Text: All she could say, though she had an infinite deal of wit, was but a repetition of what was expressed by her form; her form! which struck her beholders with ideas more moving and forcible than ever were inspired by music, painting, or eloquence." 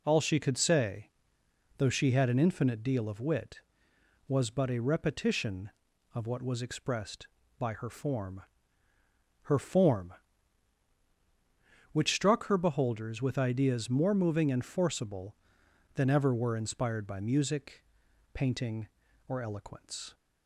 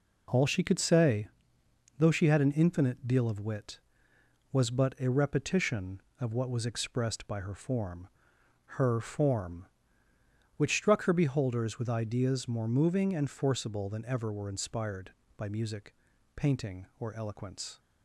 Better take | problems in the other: neither | none

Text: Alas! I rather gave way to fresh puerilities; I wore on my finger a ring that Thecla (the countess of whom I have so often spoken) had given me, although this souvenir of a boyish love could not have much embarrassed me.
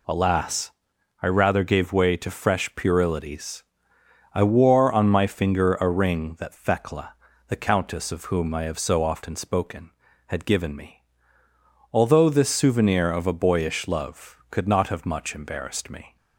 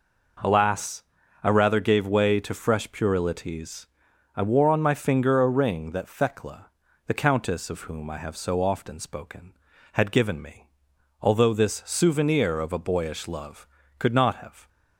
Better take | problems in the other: first | stops before "much embarrassed me"; at 14.6 s

